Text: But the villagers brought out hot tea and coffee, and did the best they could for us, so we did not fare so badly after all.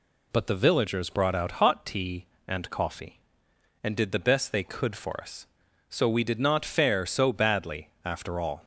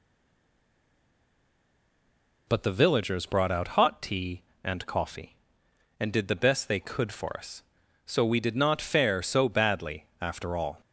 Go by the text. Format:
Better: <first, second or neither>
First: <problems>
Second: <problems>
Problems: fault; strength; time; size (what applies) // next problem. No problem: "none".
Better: first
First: none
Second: stays silent before the first word; until 2.4 s; 2.4 s long